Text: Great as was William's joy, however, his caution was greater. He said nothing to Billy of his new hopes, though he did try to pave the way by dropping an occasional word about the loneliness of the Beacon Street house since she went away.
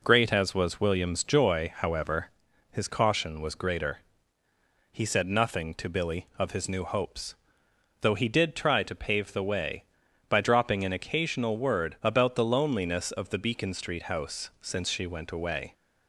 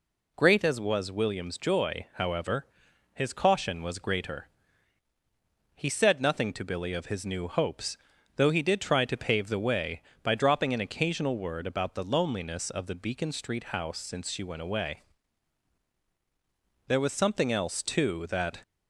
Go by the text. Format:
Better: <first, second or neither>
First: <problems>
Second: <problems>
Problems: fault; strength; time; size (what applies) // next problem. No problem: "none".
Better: first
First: none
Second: goes on to say "There was something else too that"; strong; from 16.8 s on; 1.7 s long